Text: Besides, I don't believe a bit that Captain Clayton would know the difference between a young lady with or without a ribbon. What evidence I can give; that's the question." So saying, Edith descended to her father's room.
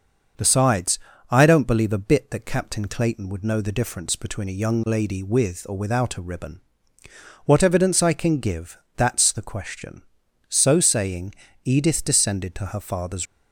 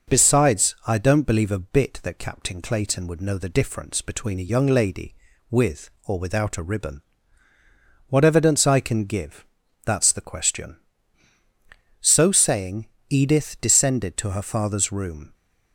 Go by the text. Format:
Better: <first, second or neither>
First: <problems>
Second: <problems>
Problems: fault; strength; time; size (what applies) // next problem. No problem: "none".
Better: second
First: starts louder than the rest; until 1.6 s; 6.5 dB // stops before "room"; at 13.2 s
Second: none